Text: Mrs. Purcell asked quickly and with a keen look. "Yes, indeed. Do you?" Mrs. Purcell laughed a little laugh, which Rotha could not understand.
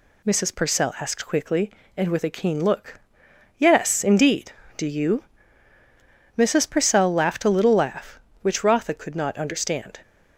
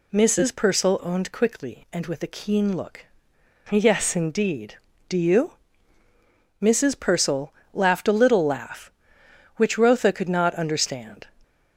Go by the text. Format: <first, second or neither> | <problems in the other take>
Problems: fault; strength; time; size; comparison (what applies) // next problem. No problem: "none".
first | says "owned" for "asked"; at 1.0 s // pauses between "Purcell" and "laughed"; slight; at 7.5 s; 0.22 s long